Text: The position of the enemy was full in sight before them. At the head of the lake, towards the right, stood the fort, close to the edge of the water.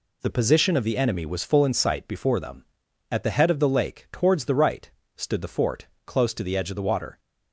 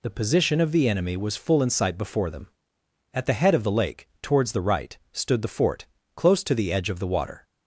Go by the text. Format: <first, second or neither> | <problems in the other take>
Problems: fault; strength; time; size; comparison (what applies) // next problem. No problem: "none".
neither | none